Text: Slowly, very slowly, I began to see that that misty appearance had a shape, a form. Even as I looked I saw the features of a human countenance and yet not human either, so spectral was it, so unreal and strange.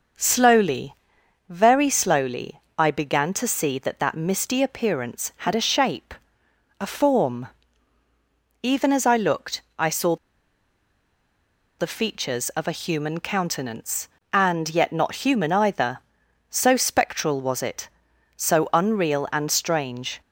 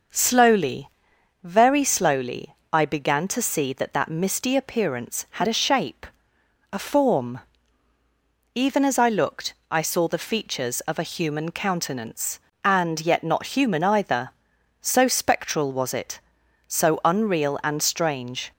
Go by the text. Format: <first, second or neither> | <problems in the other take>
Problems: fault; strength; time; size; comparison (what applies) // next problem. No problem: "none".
second | pauses between "looked" and "I"; slight; at 9.5 s; 0.18 s long; slight in the second // pauses between "saw" and "the"; strong; at 10.1 s; 1.6 s long